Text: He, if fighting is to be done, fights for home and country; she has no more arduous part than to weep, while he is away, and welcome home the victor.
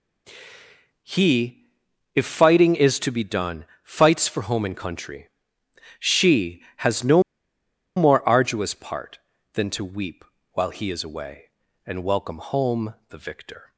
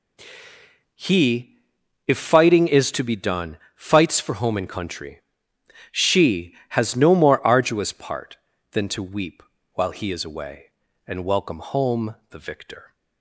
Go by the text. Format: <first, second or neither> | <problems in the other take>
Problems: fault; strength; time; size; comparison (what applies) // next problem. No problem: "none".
second | pauses between "no" and "more"; noticeable; at 7.2 s; 0.75 s long // pauses between "home" and "the"; slight; at 12.9 s; 0.16 s long; slight in the second